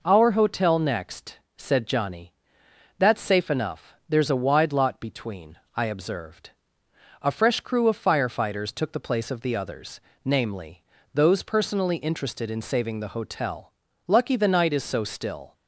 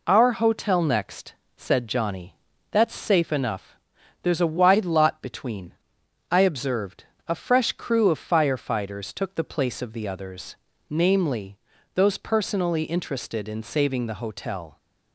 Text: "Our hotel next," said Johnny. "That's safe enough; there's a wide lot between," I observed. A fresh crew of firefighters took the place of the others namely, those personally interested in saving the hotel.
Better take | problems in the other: second | pauses between "others" and "namely"; slight; at 10.0 s; 0.24 s long; slight in the second // goes on to say "Lucky the night is so still"; from 14.0 s on; 1.4 s long

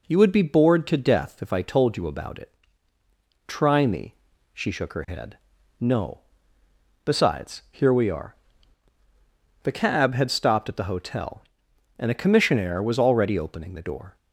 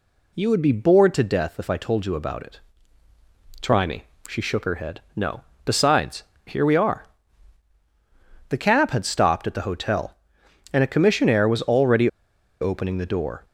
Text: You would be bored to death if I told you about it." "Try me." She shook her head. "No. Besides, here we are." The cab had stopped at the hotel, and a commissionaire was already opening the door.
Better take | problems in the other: first | pauses between "already" and "opening"; noticeable; at 12.0 s; 0.54 s long

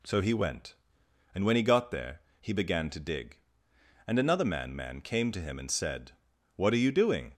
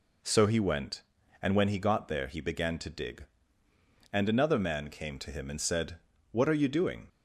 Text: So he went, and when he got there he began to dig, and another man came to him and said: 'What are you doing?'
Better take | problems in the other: second | pauses between "there" and "he"; slight; at 2.2 s; 0.20 s long // says "man" twice; at 4.7 s

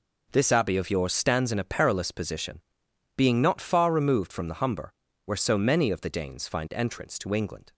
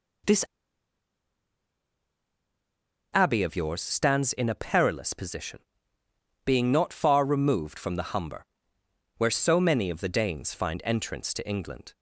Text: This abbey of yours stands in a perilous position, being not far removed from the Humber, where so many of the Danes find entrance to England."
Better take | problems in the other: first | pauses between "This" and "abbey"; strong; at 0.4 s; 2.6 s long

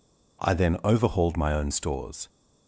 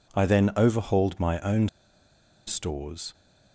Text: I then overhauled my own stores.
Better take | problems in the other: first | pauses between "own" and "stores"; noticeable; at 1.6 s; 0.78 s long

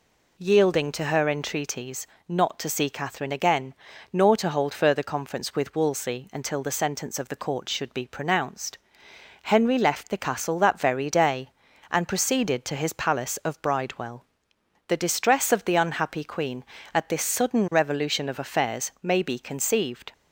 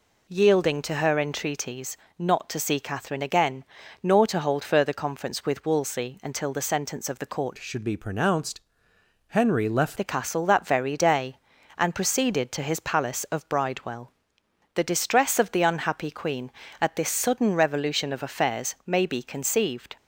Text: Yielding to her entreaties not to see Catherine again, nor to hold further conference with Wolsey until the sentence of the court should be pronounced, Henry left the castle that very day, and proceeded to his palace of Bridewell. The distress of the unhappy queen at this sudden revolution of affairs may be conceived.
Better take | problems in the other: first | pauses between "entreaties" and "not"; slight; at 1.9 s; 0.24 s long; slight in the first // changes voice from "should" to "left"; from 7.5 to 9.9 s; 2.4 s long

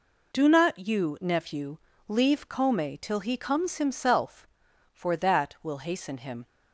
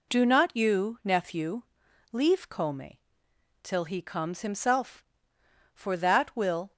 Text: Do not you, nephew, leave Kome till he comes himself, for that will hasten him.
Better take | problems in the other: first | pauses between "Kome" and "till"; noticeable; at 2.9 s; 0.66 s long // stops before "hasten him"; at 6.7 s

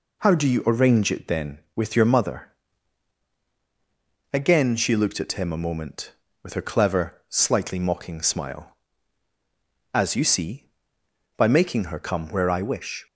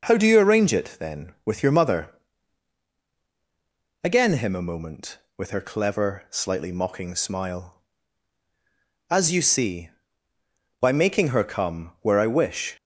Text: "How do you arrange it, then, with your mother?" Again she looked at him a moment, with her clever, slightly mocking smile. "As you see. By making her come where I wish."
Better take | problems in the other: first | skips "she looked at"; at 4.3 s

